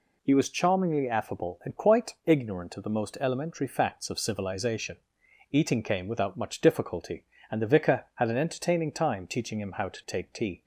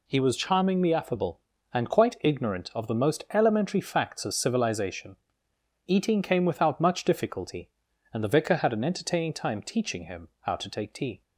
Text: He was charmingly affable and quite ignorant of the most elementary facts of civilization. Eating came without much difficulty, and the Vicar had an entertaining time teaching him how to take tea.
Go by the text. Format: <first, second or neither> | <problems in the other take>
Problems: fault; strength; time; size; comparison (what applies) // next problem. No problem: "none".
neither | none